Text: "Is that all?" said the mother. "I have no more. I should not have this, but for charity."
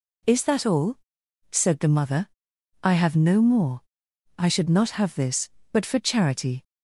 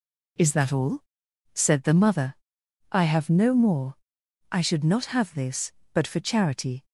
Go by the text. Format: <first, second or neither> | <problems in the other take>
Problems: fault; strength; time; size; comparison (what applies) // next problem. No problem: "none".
neither | none